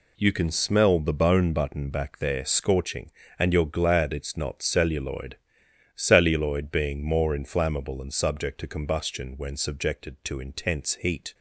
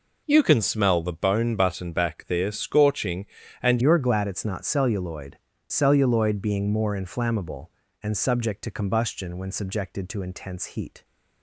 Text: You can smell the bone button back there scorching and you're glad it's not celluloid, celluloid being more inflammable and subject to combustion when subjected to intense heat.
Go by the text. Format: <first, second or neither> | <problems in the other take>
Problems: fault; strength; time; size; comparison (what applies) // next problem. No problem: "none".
first | changes voice at "you're"; from 3.8 s on; 7.2 s long